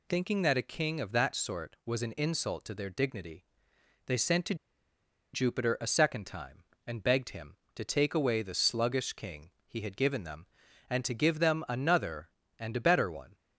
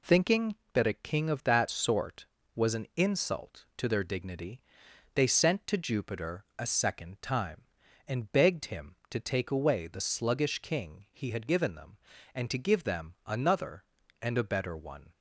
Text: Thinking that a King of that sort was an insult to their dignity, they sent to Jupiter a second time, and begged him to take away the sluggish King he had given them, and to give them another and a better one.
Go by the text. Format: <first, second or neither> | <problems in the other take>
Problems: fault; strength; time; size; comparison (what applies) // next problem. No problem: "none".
second | pauses between "to" and "Jupiter"; noticeable; at 4.5 s; 0.78 s long